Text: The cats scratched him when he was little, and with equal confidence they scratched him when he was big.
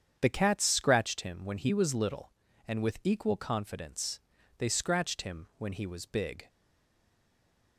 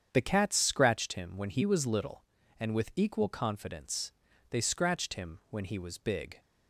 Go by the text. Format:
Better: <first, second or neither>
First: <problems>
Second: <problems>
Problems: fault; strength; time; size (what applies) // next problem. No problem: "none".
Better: second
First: starts louder than the rest; strong; until 1.2 s; 8 dB // pauses between "confidence" and "they"; at 4.1 s; 0.40 s long // stays silent after the last word; noticeable; from 6.4 s on; 1.3 s long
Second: starts louder than the rest; strong; until 1.1 s; 8 dB // pauses between "confidence" and "they"; at 4.1 s; 0.40 s long